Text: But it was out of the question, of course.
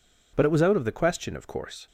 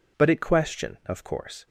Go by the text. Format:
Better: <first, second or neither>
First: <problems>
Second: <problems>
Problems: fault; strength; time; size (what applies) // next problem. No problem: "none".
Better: first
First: none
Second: skips "was out of the"; at 0.3 s